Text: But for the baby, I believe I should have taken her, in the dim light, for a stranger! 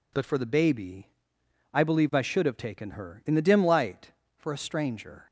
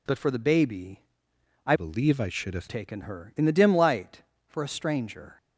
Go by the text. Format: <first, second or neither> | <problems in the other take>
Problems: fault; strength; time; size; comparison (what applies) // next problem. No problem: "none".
first | changes voice from "believe" to "have"; from 1.7 to 2.6 s; 0.9 s long